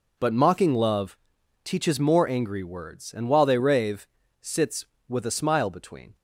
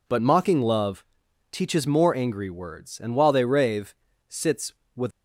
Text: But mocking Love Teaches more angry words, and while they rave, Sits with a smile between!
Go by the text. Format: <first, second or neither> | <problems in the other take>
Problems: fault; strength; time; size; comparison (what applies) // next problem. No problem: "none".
first | pauses between "Love" and "Teaches"; noticeable; at 1.0 s; 0.46 s long; noticeable in the first // stops before "a smile between"; at 5.1 s